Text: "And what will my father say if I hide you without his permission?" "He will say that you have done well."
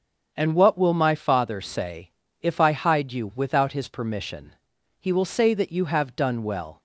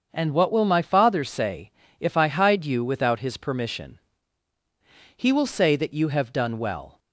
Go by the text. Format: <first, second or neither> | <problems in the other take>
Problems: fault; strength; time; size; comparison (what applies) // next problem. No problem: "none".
neither | starts louder than the rest; the same in both // pauses between "say" and "if"; slight; the same in both